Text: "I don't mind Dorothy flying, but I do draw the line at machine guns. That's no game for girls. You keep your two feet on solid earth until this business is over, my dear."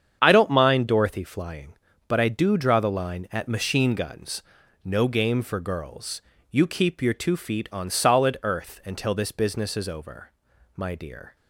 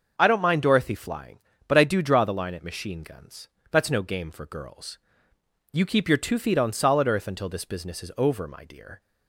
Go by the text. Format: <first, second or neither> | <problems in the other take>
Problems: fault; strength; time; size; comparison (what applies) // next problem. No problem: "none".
second | starts louder than the rest; strong; until 1.2 s; 8 dB; noticeable in the second // skips "That's"; at 4.6 s